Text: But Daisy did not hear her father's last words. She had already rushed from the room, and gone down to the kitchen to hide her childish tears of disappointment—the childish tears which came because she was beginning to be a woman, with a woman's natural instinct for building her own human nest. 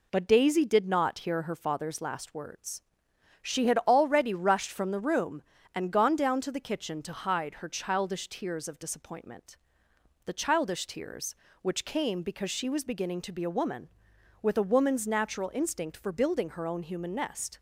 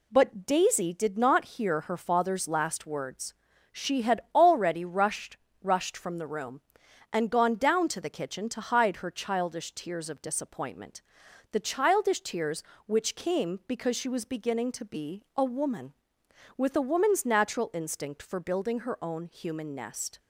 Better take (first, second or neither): first